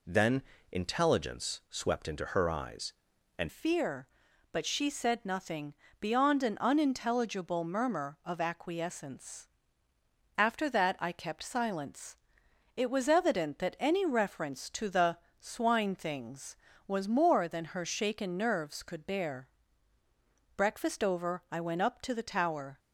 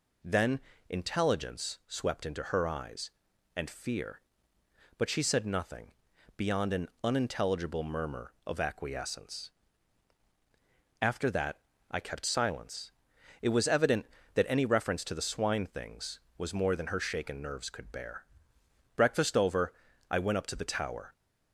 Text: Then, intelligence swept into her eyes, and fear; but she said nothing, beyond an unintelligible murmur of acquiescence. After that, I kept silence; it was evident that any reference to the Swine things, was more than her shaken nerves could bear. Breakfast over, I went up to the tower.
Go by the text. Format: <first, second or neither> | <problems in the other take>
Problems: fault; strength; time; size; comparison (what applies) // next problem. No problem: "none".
second | changes voice at "fear"; from 3.4 s on; 19.3 s long // pauses between "the" and "Swine"; slight; at 15.1 s; 0.24 s long